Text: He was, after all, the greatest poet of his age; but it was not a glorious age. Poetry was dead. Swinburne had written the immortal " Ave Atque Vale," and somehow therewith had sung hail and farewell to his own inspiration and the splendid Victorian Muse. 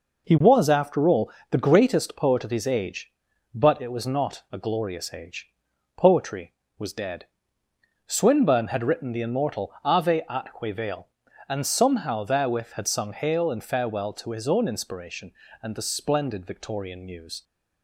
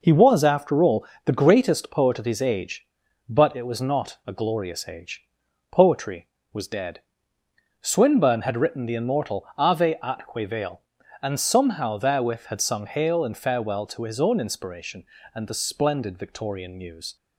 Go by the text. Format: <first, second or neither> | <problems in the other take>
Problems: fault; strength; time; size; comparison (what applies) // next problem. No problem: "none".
neither | none